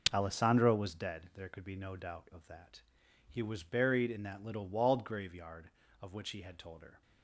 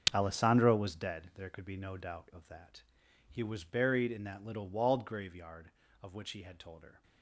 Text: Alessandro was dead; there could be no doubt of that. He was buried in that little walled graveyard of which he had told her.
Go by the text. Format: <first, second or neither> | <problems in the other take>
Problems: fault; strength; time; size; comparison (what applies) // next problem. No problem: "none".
first | gets quieter; strong; throughout; 11.5 dB